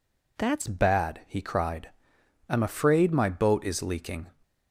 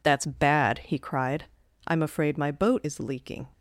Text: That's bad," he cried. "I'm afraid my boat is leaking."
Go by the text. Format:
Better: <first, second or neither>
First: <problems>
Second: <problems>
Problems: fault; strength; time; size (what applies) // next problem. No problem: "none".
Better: second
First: changes voice at "bad"; from 0.6 s on; 3.6 s long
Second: none